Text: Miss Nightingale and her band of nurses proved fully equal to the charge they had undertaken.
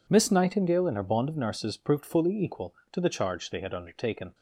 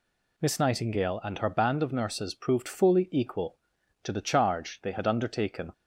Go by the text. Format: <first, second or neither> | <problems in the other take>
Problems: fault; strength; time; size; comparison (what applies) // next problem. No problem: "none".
second | says "bond" for "band"; at 1.0 s